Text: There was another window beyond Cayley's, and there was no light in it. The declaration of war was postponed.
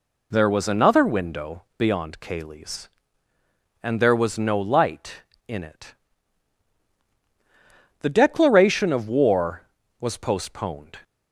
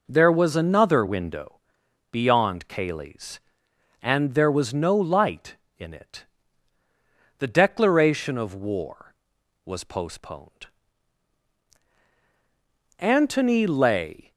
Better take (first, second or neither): first